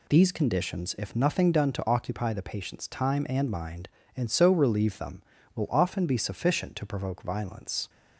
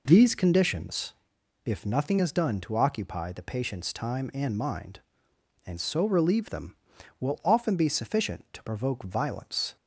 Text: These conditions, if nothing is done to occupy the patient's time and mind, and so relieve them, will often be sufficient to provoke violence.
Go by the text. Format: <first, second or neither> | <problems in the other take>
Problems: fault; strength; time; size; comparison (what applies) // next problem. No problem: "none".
second | skips "is"; at 1.5 s